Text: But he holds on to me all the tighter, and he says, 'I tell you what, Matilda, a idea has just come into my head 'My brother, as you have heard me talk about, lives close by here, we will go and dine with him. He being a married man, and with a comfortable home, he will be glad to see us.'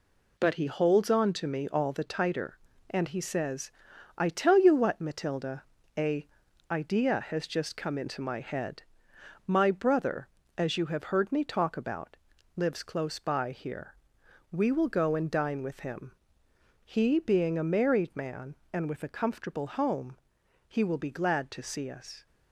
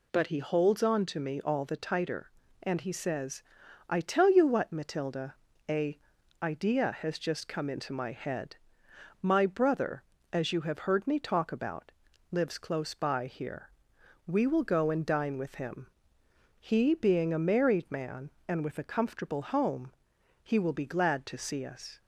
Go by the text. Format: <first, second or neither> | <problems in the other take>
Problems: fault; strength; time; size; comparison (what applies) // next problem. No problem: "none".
second | gets quieter; throughout; 6.5 dB // pauses between "a" and "idea"; at 6.2 s; 0.44 s long; also in the second // pauses between "head" and "My"; noticeable; at 8.8 s; 0.62 s long; noticeable in the second